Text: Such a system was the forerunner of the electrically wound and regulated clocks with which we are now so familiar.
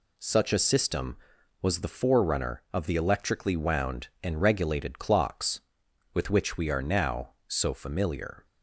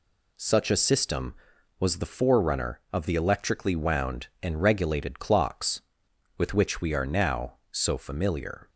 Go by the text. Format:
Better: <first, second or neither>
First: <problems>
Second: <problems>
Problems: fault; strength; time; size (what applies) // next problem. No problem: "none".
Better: neither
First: none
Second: none